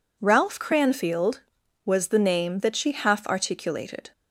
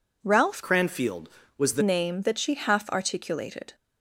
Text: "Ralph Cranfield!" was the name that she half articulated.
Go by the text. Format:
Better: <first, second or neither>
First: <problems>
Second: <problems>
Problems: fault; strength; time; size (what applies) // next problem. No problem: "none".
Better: first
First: none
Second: changes voice from "Cranfield" to "the"; from 0.6 to 1.8 s; 1.2 s long